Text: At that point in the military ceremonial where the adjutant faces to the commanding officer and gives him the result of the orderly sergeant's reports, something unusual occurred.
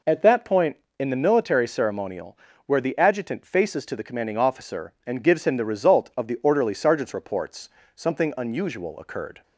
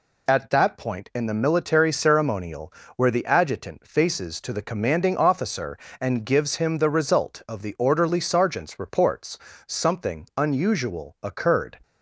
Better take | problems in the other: neither | pauses between "ceremonial" and "where"; slight; the same in both

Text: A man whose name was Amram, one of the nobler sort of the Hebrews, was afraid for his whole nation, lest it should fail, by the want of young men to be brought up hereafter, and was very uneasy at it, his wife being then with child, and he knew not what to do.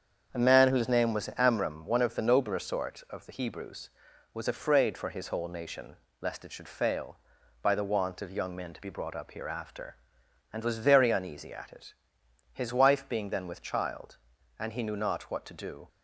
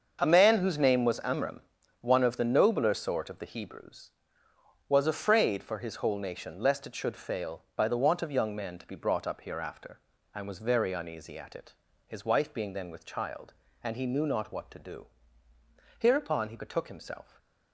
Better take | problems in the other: first | starts louder than the rest; until 1.2 s; 6.5 dB; strong in the first // goes on to say "Hereupon he betook himself"; from 15.9 s on; 1.3 s long

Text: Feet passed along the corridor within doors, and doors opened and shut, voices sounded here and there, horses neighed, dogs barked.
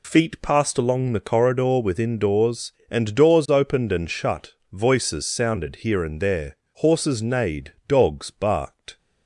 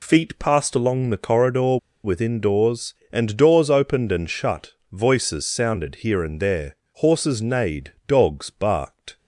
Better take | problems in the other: first | pauses between "corridor" and "within"; slight; at 1.7 s; 0.27 s long

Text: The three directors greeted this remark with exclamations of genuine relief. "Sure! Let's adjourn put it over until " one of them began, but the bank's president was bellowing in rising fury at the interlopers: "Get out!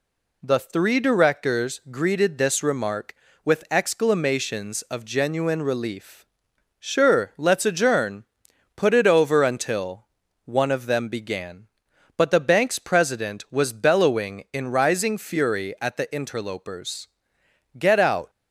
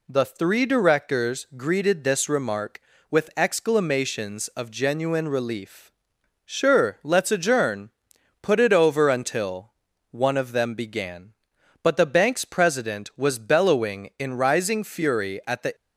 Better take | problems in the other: first | pauses between "adjourn" and "put"; noticeable; at 7.8 s; 0.52 s long; noticeable in the first // stops before "interlopers Get out"; at 15.7 s

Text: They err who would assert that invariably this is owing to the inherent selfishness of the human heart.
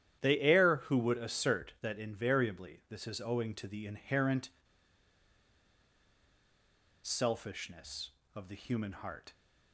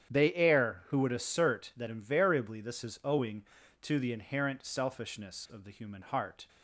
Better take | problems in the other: second | starts louder than the rest; strong; until 1.2 s; 10.5 dB; strong in the second // pauses between "inherent" and "selfishness"; strong; at 4.4 s; 2.5 s long

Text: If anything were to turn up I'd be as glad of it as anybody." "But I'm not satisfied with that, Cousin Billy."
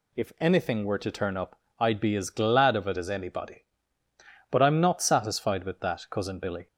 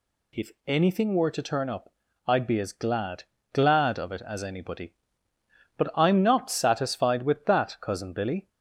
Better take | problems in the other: first | pauses between "If" and "anything"; slight; at 0.4 s; 0.16 s long // pauses between "up" and "I'd"; slight; at 1.9 s; 0.34 s long; slight in the first // says "glad" twice; at 3.5 s

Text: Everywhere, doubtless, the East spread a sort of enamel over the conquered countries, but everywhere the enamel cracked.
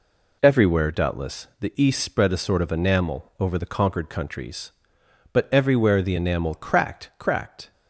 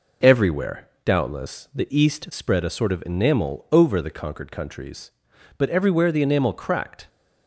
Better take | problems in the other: second | says "cracked" twice; at 7.1 s

